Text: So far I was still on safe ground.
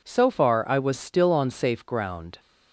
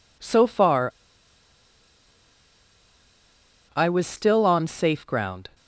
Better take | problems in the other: first | pauses between "far" and "I"; strong; at 0.9 s; 2.8 s long

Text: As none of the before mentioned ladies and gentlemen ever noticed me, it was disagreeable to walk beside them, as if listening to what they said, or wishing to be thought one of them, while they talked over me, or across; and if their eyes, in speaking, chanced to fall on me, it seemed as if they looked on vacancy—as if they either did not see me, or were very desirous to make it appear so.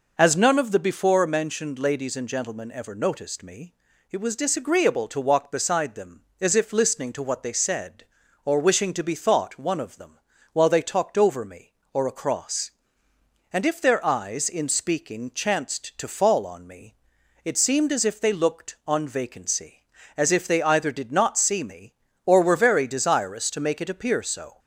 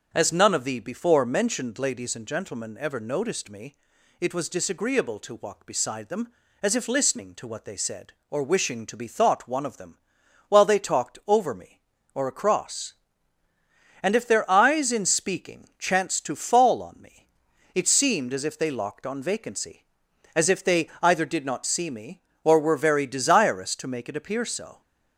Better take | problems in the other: first | starts louder than the rest; until 1.1 s; 7 dB // says "locked" for "looked"; at 18.6 s

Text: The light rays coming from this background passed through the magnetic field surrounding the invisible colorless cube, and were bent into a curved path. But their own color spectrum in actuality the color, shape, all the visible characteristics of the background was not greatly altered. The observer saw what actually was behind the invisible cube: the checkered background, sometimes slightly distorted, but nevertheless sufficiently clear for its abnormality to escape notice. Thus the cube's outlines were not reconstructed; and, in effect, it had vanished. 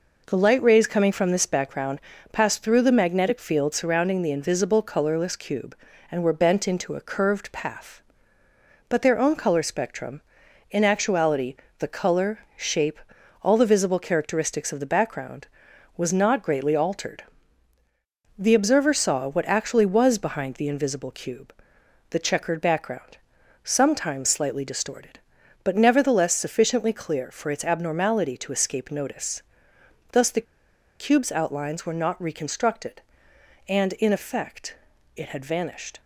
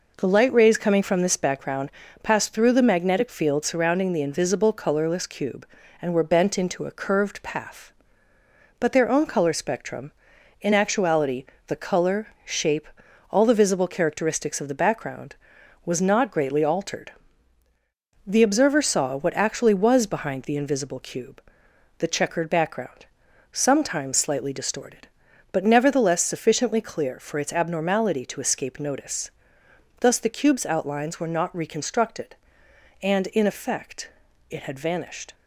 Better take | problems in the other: second | pauses between "background" and "passed"; slight; at 1.9 s; 0.32 s long; slight in the second // pauses between "actuality" and "the"; slight; at 11.5 s; 0.24 s long; slight in the second // pauses between "the" and "cube's"; noticeable; at 30.4 s; 0.54 s long

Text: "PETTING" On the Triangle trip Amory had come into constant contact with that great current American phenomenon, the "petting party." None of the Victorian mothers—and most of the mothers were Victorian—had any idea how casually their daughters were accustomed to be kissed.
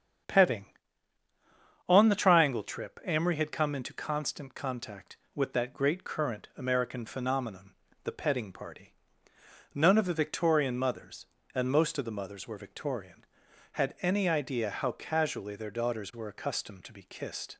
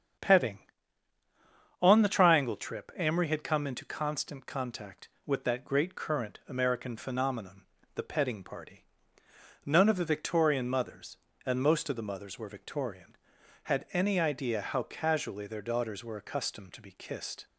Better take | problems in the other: neither | starts louder than the rest; strong; the same in both

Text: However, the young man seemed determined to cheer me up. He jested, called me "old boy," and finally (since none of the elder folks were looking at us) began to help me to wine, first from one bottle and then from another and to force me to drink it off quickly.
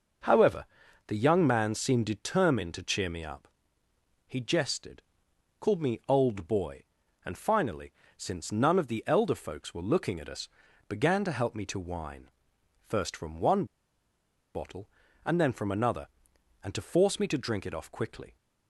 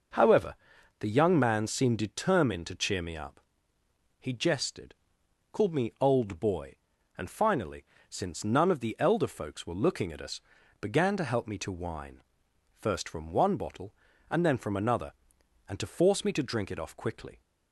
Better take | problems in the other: second | pauses between "one" and "bottle"; noticeable; at 13.6 s; 0.90 s long

